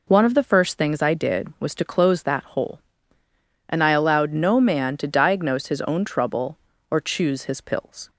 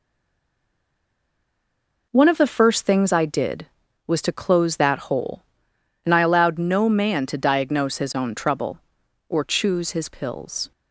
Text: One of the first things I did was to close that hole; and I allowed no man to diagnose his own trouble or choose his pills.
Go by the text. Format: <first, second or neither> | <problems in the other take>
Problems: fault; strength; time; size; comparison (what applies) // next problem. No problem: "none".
first | stays silent before the first word; until 2.1 s; 2.1 s long